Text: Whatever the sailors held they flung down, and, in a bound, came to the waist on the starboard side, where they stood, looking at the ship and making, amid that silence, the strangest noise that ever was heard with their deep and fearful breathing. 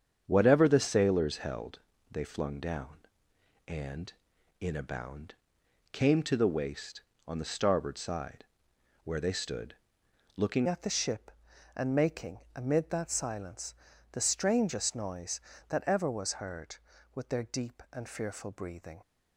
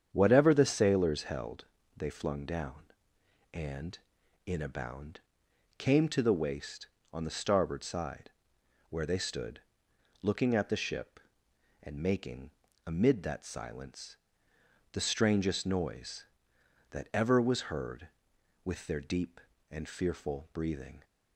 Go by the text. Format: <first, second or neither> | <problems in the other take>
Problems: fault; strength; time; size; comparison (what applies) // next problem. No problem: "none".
second | starts louder than the rest; strong; until 1.2 s; 7.5 dB; strong in the second // pauses between "held" and "they"; slight; at 1.7 s; 0.30 s long; slight in the second // changes voice at "at"; from 10.6 s on; 8.4 s long